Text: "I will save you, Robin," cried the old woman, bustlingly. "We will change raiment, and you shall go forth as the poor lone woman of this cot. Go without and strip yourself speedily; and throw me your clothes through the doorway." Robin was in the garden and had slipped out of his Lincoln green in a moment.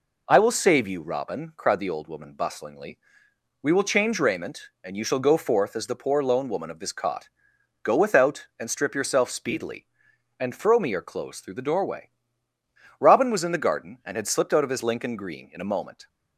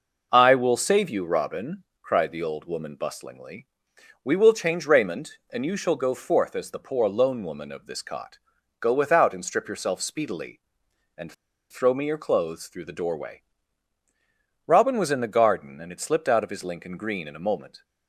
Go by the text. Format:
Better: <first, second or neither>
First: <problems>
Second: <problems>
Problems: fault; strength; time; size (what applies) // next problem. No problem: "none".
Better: first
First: none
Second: pauses between "and" and "throw"; at 11.3 s; 0.37 s long